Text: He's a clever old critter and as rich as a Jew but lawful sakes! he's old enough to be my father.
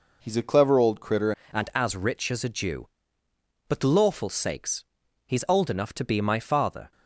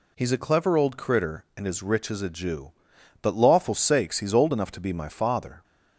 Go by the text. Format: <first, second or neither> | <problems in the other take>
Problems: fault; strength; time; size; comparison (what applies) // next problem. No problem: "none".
second | changes voice at "and"; from 1.5 s on; 5.4 s long